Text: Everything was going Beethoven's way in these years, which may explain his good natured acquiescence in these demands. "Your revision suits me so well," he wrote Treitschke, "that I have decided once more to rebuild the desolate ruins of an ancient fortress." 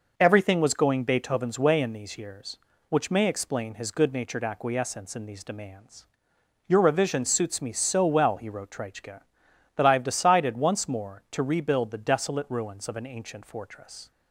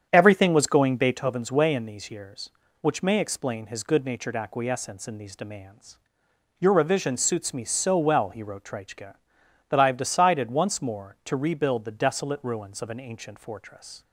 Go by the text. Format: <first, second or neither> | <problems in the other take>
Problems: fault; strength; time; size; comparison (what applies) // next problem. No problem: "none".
first | starts louder than the rest; strong; until 1.2 s; 8.5 dB